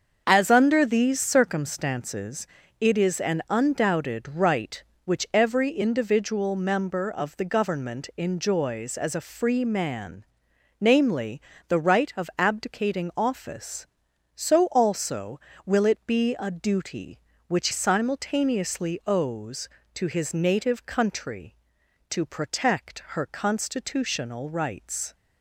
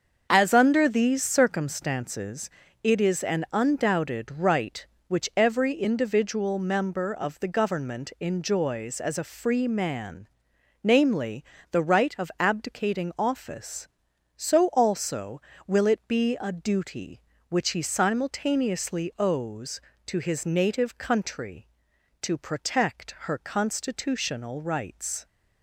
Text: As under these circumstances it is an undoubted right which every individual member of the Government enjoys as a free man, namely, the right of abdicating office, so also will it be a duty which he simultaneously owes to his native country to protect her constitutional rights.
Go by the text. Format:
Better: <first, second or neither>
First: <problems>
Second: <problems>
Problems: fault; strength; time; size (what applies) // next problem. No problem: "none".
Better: second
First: starts louder than the rest; until 1.2 s; 7 dB // pauses between "circumstances" and "it"; slight; at 2.4 s; 0.32 s long // skips "he"; at 17.6 s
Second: starts louder than the rest; until 1.3 s; 7 dB // pauses between "circumstances" and "it"; slight; at 2.4 s; 0.32 s long